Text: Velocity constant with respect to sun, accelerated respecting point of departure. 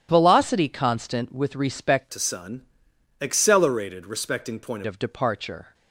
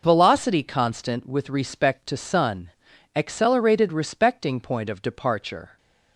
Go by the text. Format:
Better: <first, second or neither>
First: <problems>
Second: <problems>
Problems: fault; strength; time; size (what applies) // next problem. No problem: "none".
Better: second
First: starts louder than the rest; strong; until 1.1 s; 10.5 dB // changes voice from "to" to "point"; from 2.1 to 4.8 s; 2.7 s long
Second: none